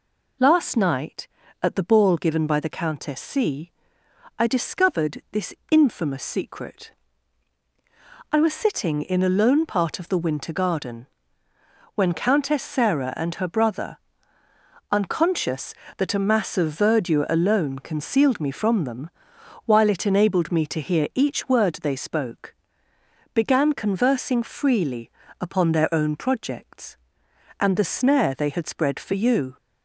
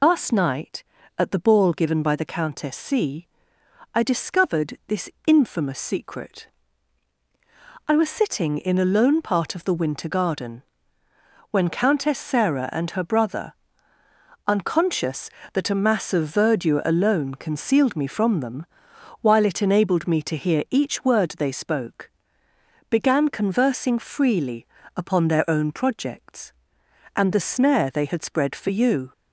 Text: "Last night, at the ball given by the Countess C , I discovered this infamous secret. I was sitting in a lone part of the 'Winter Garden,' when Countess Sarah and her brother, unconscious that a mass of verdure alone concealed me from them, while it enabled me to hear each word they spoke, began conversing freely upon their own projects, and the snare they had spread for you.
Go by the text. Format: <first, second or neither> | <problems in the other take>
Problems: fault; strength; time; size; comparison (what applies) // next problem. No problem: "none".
first | loses the start of "Last"; at 0.0 s; 65 ms // pauses between "this" and "infamous"; slight; at 5.0 s; 0.16 s long; slight in the first // pauses between "freely" and "upon"; slight; at 24.6 s; 0.28 s long; slight in the first